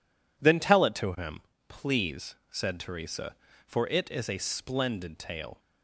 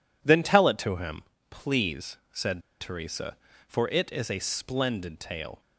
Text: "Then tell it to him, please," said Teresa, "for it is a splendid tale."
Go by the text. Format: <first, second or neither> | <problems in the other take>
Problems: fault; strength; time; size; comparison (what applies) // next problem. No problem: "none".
first | pauses between "said" and "Teresa"; slight; at 2.6 s; 0.20 s long